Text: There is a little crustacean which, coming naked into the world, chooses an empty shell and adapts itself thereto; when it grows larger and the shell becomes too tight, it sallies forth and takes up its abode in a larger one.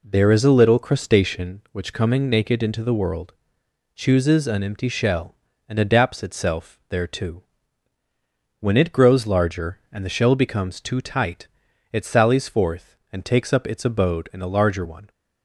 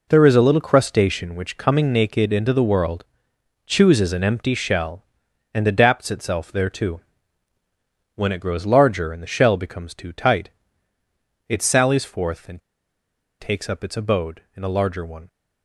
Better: first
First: none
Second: pauses between "and" and "takes"; noticeable; at 12.6 s; 0.81 s long

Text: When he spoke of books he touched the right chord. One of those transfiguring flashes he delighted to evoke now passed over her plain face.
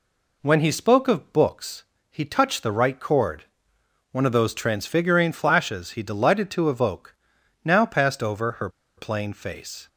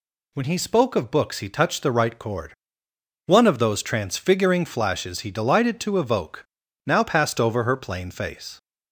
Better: second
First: pauses between "books" and "he"; slight; at 1.8 s; 0.26 s long // pauses between "evoke" and "now"; noticeable; at 7.1 s; 0.50 s long // pauses between "her" and "plain"; slight; at 8.6 s; 0.27 s long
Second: pauses between "evoke" and "now"; at 6.4 s; 0.40 s long

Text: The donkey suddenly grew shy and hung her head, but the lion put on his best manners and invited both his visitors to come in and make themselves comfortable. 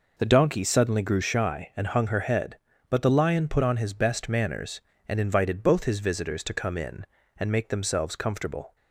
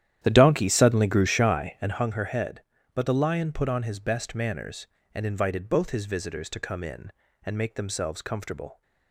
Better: first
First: none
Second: starts louder than the rest; strong; until 2.0 s; 11 dB

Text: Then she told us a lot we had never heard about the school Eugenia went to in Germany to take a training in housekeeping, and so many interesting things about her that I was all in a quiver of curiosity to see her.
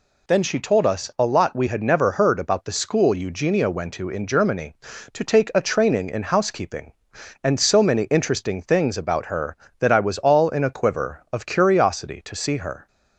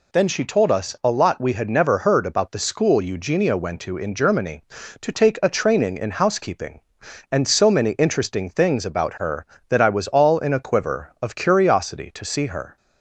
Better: neither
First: none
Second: none

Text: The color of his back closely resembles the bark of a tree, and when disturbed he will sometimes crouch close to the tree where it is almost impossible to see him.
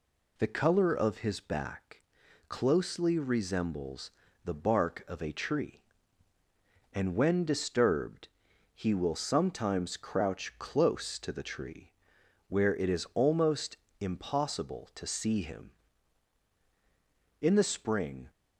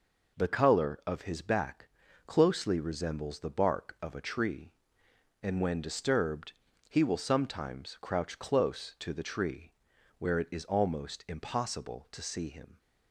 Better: second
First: pauses between "back" and "closely"; noticeable; at 2.0 s; 0.48 s long // pauses between "resembles" and "the"; slight; at 4.0 s; 0.34 s long // pauses between "disturbed" and "he"; noticeable; at 8.2 s; 0.46 s long // pauses between "tree" and "where"; noticeable; at 11.9 s; 0.56 s long // pauses between "almost" and "impossible"; slight; at 13.7 s; 0.24 s long // goes on to say "In the spring"; noticeable; from 17.3 s on; 0.90 s long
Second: pauses between "back" and "closely"; at 1.8 s; 0.38 s long // pauses between "disturbed" and "he"; slight; at 6.5 s; 0.36 s long // pauses between "tree" and "where"; noticeable; at 9.7 s; 0.46 s long

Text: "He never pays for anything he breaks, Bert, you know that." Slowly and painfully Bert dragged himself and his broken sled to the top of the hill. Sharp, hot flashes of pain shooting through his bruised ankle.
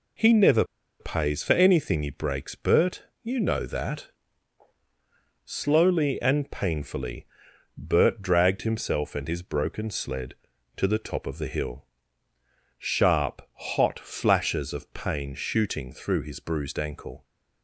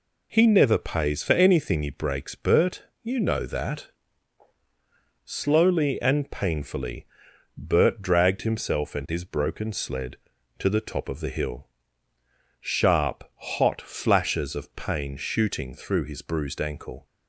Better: second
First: pauses between "never" and "pays"; at 0.6 s; 0.36 s long // pauses between "painfully" and "Bert"; noticeable; at 7.2 s; 0.52 s long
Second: pauses between "painfully" and "Bert"; noticeable; at 7.0 s; 0.52 s long

